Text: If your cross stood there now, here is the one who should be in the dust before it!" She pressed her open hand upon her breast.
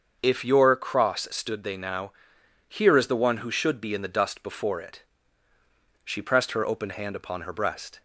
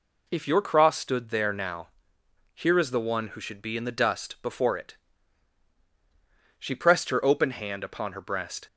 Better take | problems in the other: second | starts louder than the rest; until 1.2 s; 6.5 dB // says "they" for "there"; at 1.6 s

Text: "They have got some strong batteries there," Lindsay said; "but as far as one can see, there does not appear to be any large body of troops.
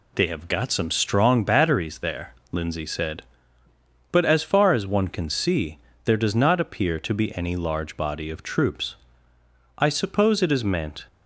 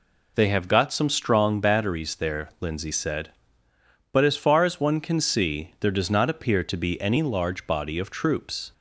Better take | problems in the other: second | goes on to say "I suppose it is meant"; noticeable; from 9.7 s on; 1.2 s long

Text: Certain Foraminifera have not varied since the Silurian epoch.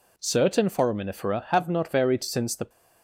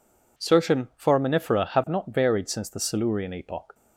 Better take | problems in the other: second | stops before "Silurian epoch"; at 2.6 s

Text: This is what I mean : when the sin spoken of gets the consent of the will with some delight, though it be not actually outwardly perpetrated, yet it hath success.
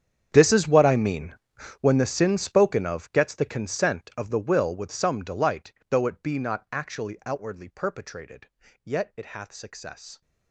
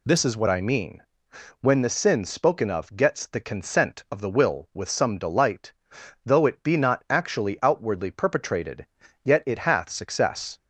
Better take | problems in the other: second | gets quieter; strong; throughout; 19 dB

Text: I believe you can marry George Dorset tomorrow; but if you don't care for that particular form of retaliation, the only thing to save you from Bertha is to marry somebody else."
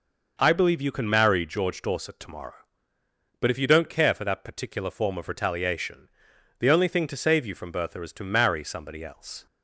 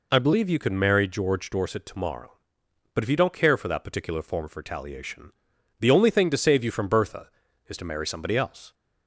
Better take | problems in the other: neither | none

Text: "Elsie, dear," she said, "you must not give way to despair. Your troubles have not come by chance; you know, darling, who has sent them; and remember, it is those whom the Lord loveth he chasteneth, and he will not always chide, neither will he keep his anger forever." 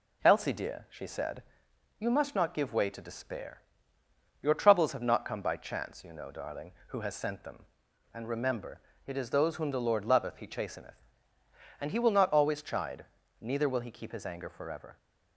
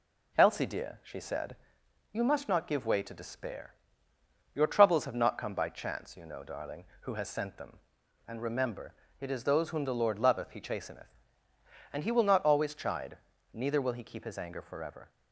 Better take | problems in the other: neither | none

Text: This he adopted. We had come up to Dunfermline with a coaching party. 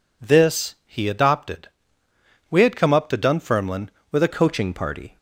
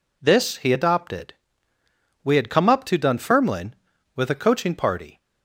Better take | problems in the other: second | changes voice at "coaching"; from 4.2 s on; 0.9 s long

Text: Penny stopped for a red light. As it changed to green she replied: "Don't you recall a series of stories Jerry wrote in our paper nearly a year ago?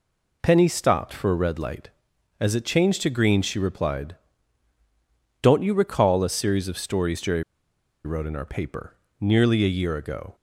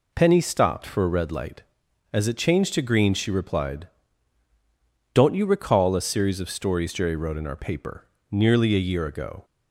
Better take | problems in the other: second | pauses between "Jerry" and "wrote"; noticeable; at 7.4 s; 0.61 s long // pauses between "paper" and "nearly"; slight; at 8.9 s; 0.24 s long; slight in the second

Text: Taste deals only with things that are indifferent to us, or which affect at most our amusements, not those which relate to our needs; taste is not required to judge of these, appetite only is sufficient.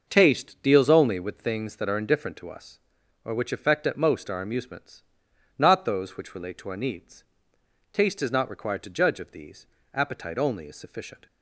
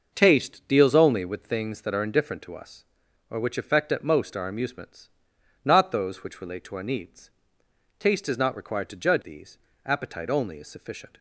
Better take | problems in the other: first | skips "of"; at 9.2 s

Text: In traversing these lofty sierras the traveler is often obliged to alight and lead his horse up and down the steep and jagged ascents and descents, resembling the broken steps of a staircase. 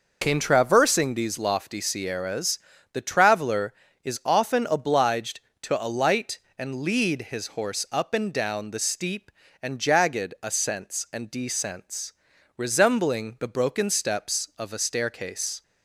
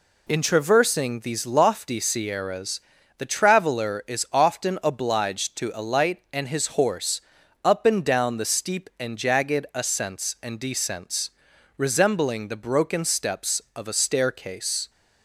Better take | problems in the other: first | pauses between "sierras" and "the"; slight; at 2.8 s; 0.34 s long; slight in the first // skips "lead"; at 6.4 s // pauses between "horse" and "up"; at 7.2 s; 0.42 s long

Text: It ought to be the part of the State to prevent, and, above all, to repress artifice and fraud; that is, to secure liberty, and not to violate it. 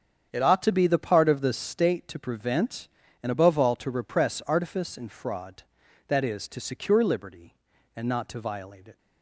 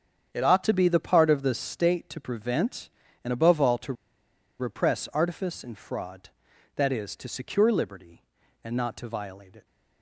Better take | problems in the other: first | starts louder than the rest; strong; until 1.3 s; 8 dB; strong in the first // pauses between "to" and "repress"; noticeable; at 3.9 s; 0.66 s long

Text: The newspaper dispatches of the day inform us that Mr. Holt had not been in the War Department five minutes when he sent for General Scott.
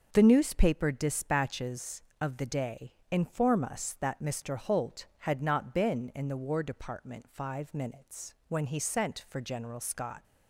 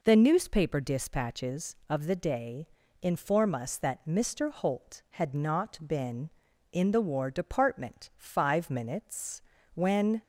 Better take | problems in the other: first | pauses between "day" and "inform"; at 2.6 s; 0.38 s long; slight in the first // pauses between "minutes" and "when"; slight; at 9.4 s; 0.32 s long // stops before "he sent for General Scott"; at 10.2 s

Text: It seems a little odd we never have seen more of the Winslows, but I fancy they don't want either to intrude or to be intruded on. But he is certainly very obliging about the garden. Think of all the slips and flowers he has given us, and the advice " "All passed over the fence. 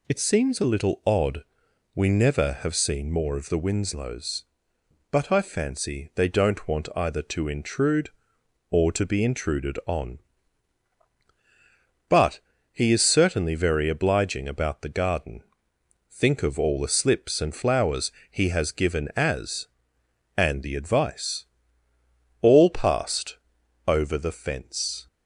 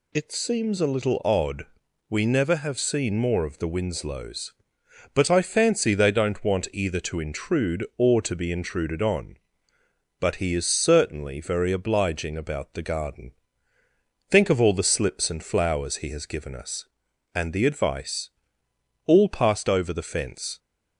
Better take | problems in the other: second | pauses between "odd" and "we"; noticeable; at 1.4 s; 0.52 s long; also in the second // pauses between "But" and "he"; slight; at 12.3 s; 0.32 s long // pauses between "flowers" and "he"; slight; at 18.1 s; 0.20 s long // says "as" for "us"; at 19.1 s // pauses between "passed" and "over"; noticeable; at 23.3 s; 0.50 s long

